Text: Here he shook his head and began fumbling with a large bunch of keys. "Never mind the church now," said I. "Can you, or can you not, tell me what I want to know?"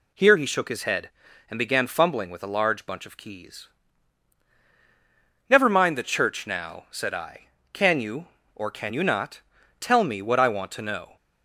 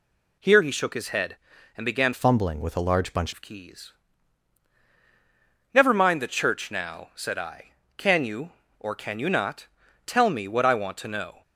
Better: first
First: none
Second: changes voice from "fumbling" to "bunch"; from 2.1 to 3.3 s; 1.2 s long

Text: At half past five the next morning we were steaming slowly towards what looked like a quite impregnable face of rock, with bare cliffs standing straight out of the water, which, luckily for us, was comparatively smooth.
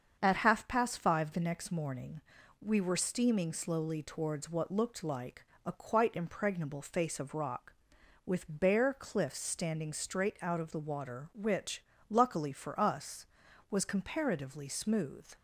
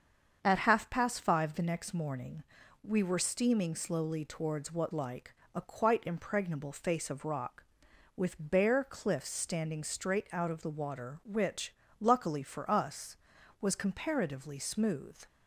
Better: first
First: starts louder than the rest; until 1.2 s; 7 dB // pauses between "morning" and "we"; at 2.2 s; 0.38 s long // pauses between "like" and "a"; slight; at 5.4 s; 0.18 s long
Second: starts louder than the rest; until 1.4 s; 7 dB // pauses between "morning" and "we"; at 2.4 s; 0.38 s long // skips "looked"; at 4.9 s // pauses between "like" and "a"; slight; at 5.3 s; 0.18 s long

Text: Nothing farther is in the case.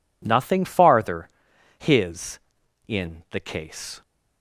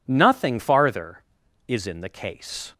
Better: second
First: says "his" for "is"; at 1.7 s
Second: none

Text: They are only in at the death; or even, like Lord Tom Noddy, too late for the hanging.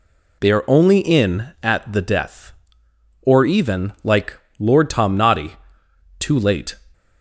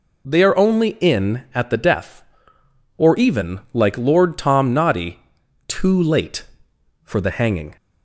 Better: second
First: pauses between "like" and "Lord"; slight; at 4.3 s; 0.18 s long // stops before "for the hanging"; at 6.9 s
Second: none

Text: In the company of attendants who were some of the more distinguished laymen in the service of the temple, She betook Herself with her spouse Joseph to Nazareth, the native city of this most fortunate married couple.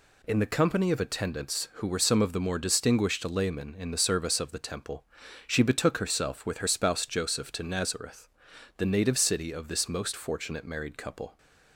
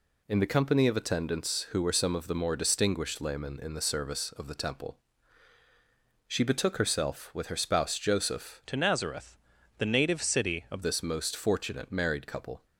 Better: first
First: none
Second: changes voice from "to" to "of"; from 8.6 to 10.8 s; 2.2 s long

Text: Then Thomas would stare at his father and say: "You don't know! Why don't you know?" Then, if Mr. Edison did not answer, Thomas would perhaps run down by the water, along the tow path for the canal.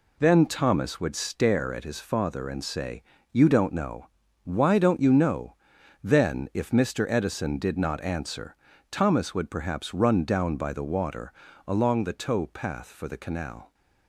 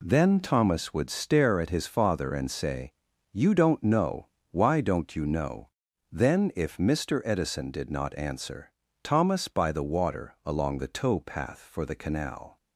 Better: first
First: none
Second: skips "would perhaps run down"; at 9.4 s

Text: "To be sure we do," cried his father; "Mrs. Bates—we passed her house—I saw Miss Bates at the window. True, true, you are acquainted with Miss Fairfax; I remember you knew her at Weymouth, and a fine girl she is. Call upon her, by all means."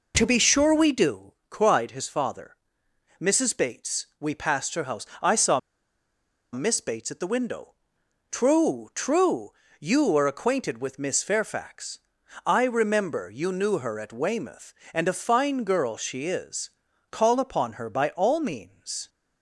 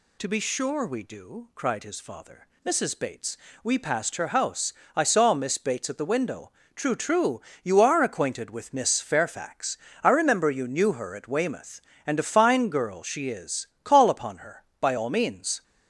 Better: second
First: pauses between "saw" and "Miss"; noticeable; at 5.5 s; 0.92 s long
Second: none

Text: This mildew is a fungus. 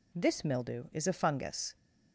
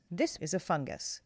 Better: first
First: none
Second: skips "mildew"; at 0.3 s

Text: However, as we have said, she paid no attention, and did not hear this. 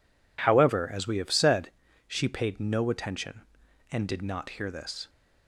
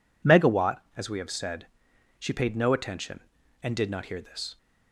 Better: first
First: none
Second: says "Megawatt" for "However"; at 0.2 s

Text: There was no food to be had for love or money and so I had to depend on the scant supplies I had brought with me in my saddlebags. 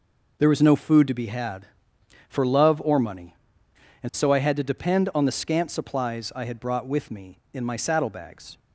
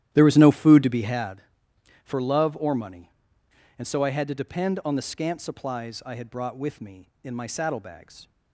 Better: first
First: none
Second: starts louder than the rest; strong; until 1.4 s; 12 dB

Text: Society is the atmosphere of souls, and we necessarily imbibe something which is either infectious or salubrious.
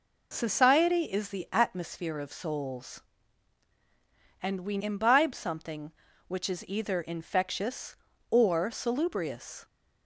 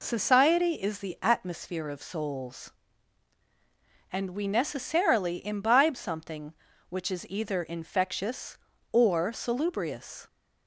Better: second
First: skips "necessarily"; at 4.8 s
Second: none

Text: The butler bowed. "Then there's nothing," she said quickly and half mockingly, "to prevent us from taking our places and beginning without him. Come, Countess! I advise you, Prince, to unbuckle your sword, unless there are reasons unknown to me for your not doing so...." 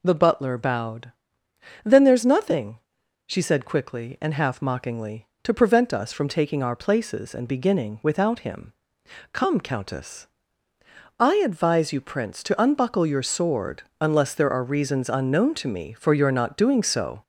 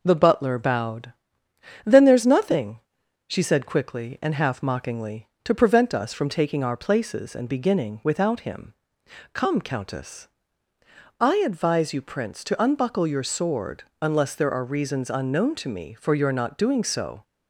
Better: second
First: gets louder; noticeable; throughout; 4 dB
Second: none

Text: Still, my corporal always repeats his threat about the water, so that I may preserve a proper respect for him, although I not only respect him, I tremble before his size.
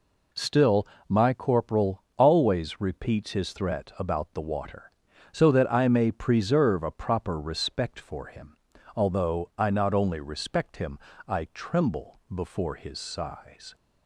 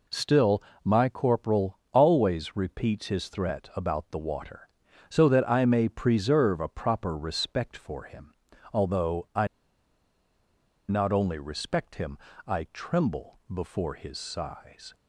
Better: first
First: none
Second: pauses between "I" and "not"; strong; at 9.4 s; 1.4 s long

